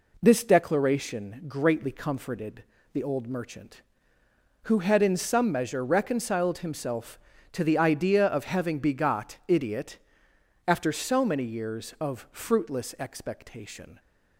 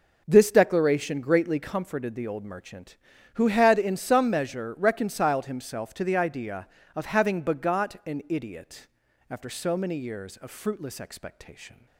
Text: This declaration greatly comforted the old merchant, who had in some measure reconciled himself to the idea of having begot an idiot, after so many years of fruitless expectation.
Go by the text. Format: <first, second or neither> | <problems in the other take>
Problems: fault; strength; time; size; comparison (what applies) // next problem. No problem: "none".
second | pauses between "comforted" and "the"; slight; at 2.6 s; 0.30 s long // skips "an"; at 9.4 s